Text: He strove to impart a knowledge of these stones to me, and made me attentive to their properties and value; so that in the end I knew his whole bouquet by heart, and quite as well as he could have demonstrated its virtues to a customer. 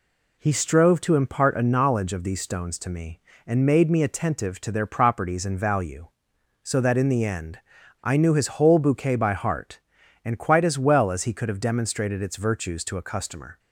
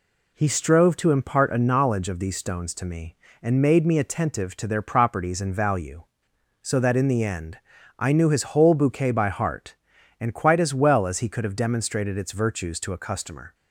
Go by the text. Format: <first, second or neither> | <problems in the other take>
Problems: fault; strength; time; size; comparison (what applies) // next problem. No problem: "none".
neither | pauses between "end" and "I"; the same in both